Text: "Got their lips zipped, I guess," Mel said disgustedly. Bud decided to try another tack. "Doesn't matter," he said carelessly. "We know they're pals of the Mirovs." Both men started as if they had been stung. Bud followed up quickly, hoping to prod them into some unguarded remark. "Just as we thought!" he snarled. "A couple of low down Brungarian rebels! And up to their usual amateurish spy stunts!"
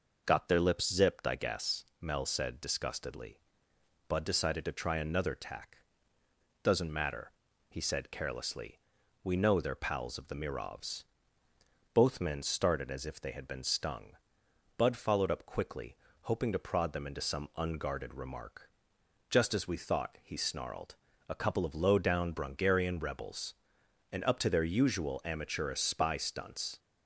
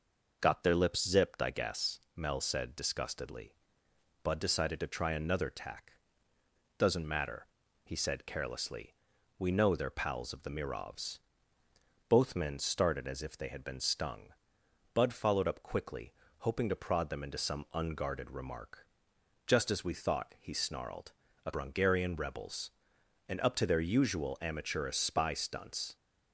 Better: first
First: none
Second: skips "couple of low down"; at 21.5 s

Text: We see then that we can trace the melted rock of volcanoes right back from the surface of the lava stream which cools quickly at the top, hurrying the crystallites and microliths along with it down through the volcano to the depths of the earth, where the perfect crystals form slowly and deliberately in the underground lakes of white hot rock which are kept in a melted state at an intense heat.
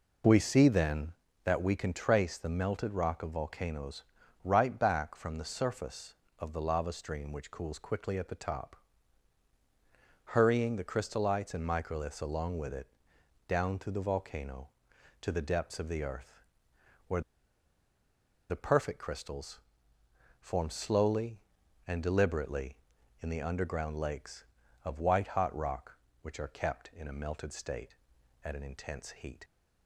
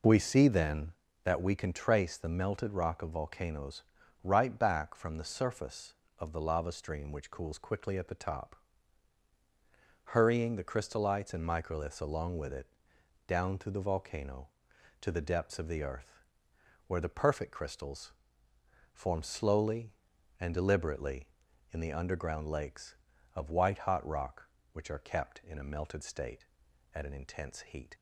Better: second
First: pauses between "volcanoes" and "right"; at 4.0 s; 0.42 s long // pauses between "it" and "down"; noticeable; at 12.8 s; 0.60 s long // pauses between "where" and "the"; strong; at 17.2 s; 1.2 s long // pauses between "crystals" and "form"; noticeable; at 19.6 s; 0.80 s long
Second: pauses between "volcanoes" and "right"; at 3.8 s; 0.42 s long // pauses between "it" and "down"; noticeable; at 12.6 s; 0.60 s long // pauses between "crystals" and "form"; noticeable; at 18.1 s; 0.80 s long

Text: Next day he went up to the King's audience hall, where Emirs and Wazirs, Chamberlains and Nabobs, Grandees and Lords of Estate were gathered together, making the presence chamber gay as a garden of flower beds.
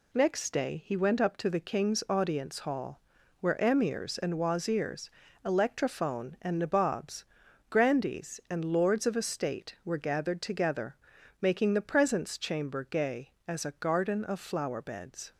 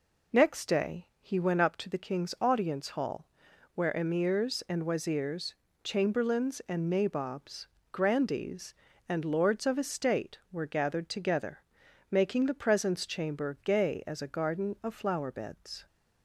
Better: second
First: says "Electrophone" for "Chamberlains"; at 5.4 s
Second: none

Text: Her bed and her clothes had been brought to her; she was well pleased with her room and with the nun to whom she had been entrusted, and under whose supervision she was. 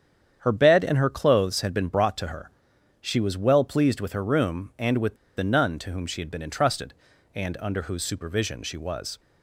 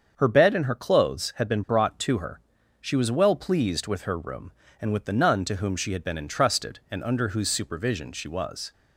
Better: second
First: starts louder than the rest; strong; until 1.4 s; 8.5 dB // pauses between "with" and "the"; slight; at 5.1 s; 0.20 s long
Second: starts louder than the rest; until 1.1 s; 7 dB

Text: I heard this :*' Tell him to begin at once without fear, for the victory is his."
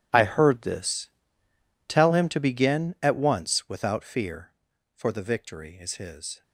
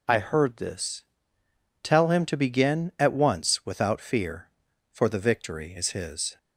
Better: second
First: gets quieter; throughout; 6.5 dB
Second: none

